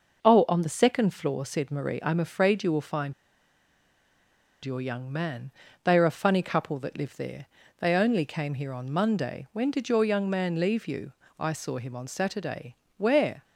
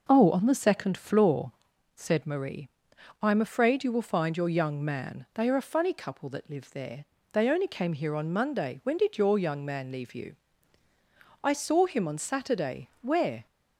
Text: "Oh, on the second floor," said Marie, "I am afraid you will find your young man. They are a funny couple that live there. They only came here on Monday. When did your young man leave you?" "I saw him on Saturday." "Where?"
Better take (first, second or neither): second